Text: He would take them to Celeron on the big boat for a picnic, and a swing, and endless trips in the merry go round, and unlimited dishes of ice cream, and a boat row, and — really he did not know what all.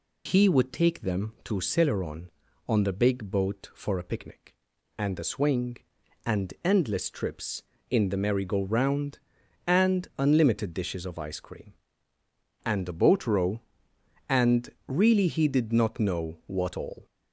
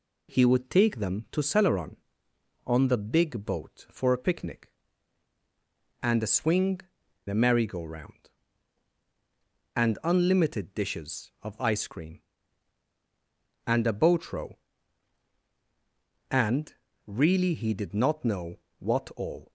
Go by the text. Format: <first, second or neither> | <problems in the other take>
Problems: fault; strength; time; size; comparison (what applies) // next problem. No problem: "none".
first | skips "and endless trips in"; at 7.0 s // pauses between "know" and "what"; slight; at 18.5 s; 0.24 s long